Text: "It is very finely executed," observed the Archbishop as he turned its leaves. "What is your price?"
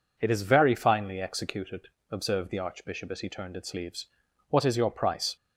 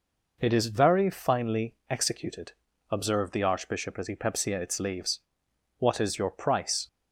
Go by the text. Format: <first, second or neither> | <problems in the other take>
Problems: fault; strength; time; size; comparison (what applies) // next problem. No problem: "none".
first | says "pepsia" for "turned"; at 4.1 s